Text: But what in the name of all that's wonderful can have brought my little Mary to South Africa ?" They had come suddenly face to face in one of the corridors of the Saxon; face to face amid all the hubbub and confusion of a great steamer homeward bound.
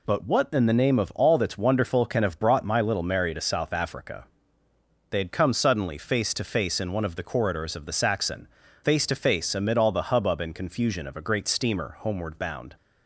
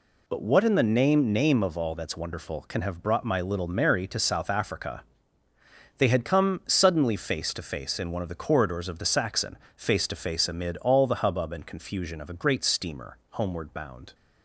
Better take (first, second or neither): first